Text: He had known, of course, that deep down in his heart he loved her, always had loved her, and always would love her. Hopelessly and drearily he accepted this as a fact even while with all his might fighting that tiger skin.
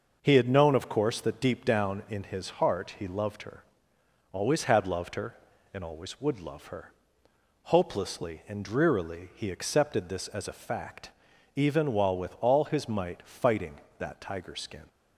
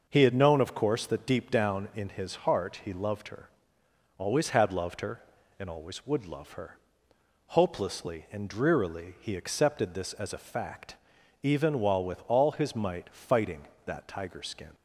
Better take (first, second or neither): neither